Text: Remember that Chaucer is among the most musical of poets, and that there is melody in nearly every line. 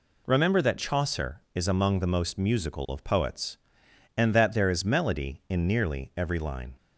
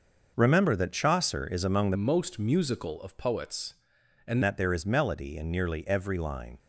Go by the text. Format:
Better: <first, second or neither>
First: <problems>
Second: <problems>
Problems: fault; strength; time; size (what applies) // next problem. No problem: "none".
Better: first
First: none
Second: starts louder than the rest; until 1.3 s; 6 dB // changes voice from "most" to "and"; from 1.9 to 4.4 s; 2.5 s long